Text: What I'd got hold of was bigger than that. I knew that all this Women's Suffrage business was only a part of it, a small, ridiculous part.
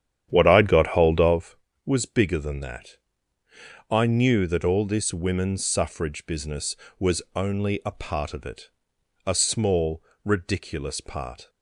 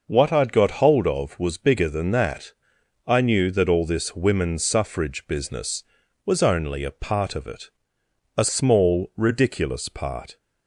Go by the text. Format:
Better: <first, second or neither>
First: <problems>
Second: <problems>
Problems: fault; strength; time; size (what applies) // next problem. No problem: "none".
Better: second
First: starts louder than the rest; strong; until 1.5 s; 9.5 dB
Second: none